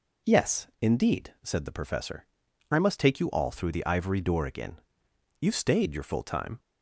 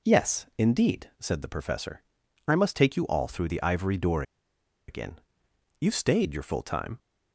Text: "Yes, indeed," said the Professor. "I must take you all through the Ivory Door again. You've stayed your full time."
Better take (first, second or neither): first